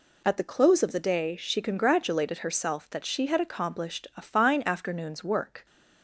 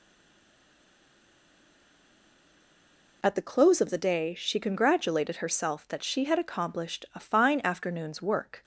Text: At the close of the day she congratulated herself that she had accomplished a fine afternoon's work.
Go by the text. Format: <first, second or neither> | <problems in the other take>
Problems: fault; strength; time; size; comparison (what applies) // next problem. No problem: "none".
first | stays silent before the first word; strong; until 3.2 s; 3.2 s long